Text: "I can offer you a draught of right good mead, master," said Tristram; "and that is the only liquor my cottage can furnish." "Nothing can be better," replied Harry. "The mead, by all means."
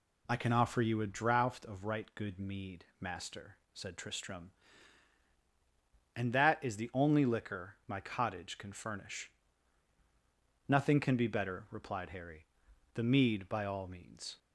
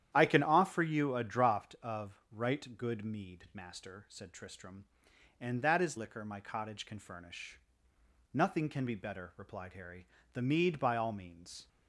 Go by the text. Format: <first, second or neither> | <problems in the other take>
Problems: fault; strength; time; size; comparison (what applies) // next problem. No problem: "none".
first | starts louder than the rest; strong; until 1.1 s; 10.5 dB // skips "the only"; at 5.9 s